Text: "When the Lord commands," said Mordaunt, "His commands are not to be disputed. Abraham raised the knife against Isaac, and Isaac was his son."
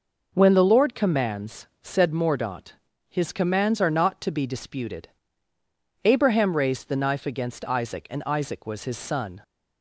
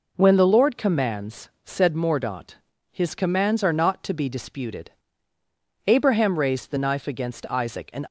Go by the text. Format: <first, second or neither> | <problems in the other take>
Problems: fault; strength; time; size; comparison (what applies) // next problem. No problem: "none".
first | stops before "Isaac was his son"; at 8.0 s